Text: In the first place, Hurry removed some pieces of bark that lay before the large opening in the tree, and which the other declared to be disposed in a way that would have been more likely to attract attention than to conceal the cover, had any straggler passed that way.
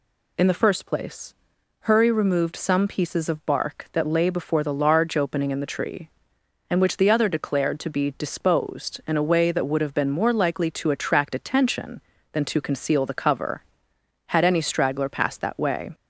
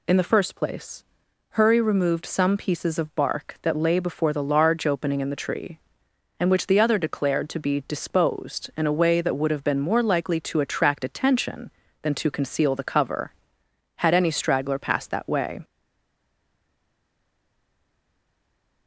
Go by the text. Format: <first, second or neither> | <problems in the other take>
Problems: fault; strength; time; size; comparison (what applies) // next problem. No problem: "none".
first | stays silent after the last word; strong; from 15.6 s on; 3.2 s long